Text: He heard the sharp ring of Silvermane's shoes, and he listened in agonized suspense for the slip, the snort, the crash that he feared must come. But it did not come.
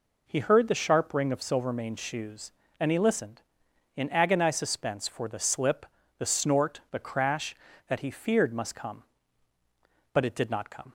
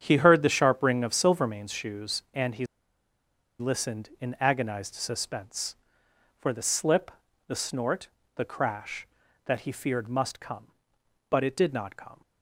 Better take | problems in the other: first | starts louder than the rest; strong; until 1.0 s; 8 dB // pauses between "he" and "listened"; noticeable; at 2.6 s; 0.93 s long

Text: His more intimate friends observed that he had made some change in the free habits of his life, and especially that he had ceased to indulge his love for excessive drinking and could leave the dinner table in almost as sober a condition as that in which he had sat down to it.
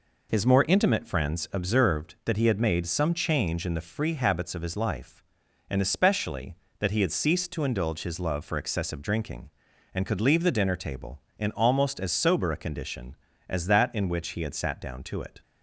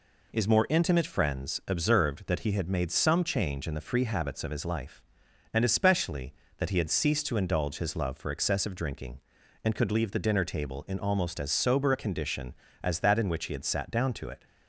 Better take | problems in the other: neither | none

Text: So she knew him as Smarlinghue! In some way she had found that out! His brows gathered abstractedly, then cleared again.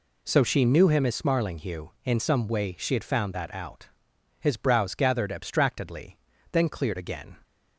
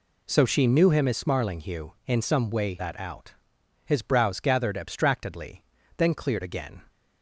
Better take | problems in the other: first | skips "she had found"; at 2.7 s

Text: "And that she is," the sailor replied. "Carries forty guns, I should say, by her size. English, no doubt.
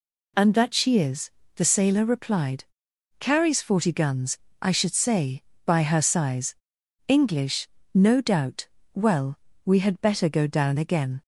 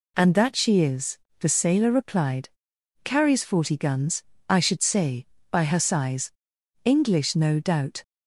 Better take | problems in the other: second | goes on to say "Well we had better go down again"; strong; from 8.9 s on; 2.2 s long

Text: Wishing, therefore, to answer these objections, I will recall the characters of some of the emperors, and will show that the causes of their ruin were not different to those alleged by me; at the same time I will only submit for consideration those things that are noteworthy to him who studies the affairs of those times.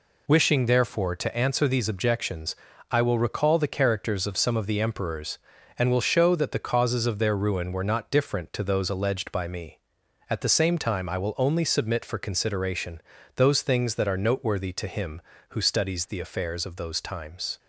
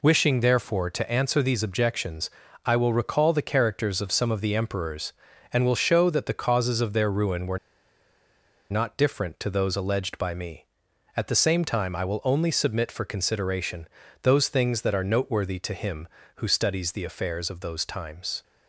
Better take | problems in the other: first | pauses between "were" and "not"; at 7.5 s; 1.1 s long // pauses between "consideration" and "those"; slight; at 13.8 s; 0.34 s long; slight in the first

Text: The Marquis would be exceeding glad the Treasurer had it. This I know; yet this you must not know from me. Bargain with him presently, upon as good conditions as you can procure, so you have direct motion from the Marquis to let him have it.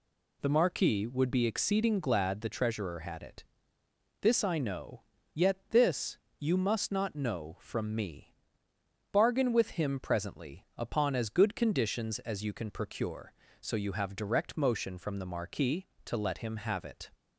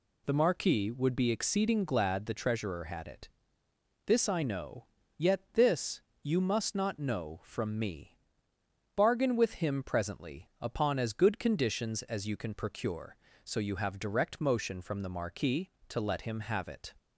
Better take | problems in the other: neither | pauses between "this" and "you"; slight; the same in both

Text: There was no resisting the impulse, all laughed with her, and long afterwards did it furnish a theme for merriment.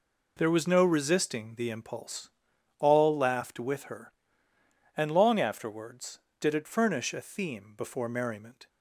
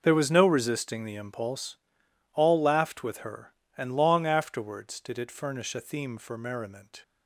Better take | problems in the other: second | says "before" for "for"; at 7.7 s

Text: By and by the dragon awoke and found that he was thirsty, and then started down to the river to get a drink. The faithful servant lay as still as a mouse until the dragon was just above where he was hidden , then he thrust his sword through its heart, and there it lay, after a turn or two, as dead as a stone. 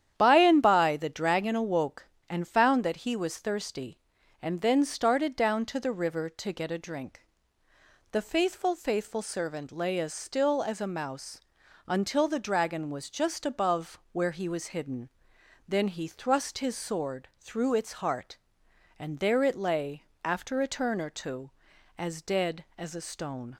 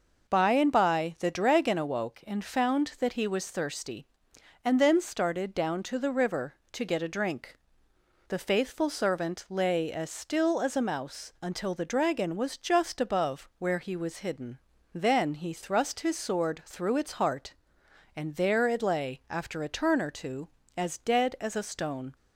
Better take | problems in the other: second | starts louder than the rest; strong; until 1.1 s; 10 dB // says "faithful" twice; at 8.7 s // pauses between "mouse" and "until"; noticeable; at 11.4 s; 0.48 s long

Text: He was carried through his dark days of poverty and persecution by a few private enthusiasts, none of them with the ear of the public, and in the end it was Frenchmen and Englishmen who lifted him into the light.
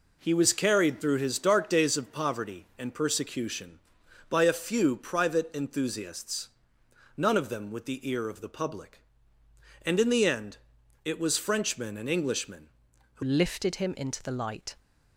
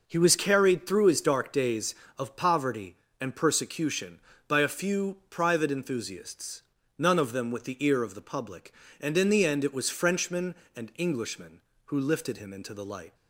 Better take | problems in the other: second | pauses between "end" and "it"; noticeable; at 10.5 s; 0.48 s long // changes voice at "lifted"; from 13.2 s on; 1.5 s long

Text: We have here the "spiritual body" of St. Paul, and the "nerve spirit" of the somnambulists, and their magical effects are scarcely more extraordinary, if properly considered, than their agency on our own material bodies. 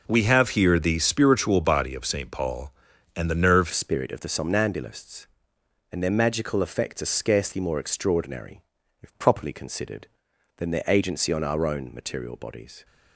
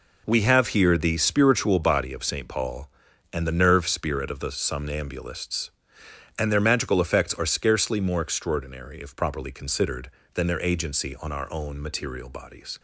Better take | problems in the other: second | changes voice at "spirit"; from 3.7 s on; 9.1 s long

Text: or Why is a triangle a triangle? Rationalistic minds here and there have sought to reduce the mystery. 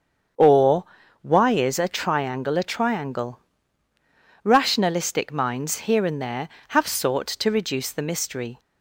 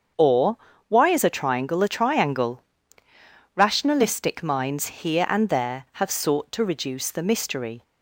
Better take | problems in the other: neither | starts louder than the rest; the same in both // pauses between "or" and "Why"; the same in both

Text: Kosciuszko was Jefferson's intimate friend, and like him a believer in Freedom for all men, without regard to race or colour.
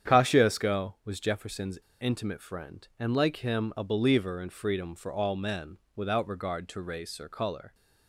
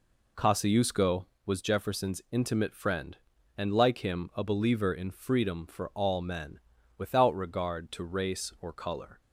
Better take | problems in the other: second | starts louder than the rest; strong; until 1.1 s; 8.5 dB // pauses between "Jefferson's" and "intimate"; slight; at 1.8 s; 0.20 s long

